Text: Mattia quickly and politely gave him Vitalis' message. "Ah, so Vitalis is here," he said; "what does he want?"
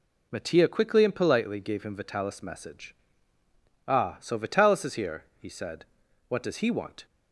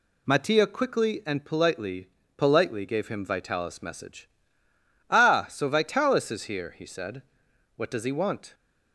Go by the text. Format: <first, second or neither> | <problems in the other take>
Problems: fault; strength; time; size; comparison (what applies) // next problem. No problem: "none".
first | says "politely" twice; at 2.3 s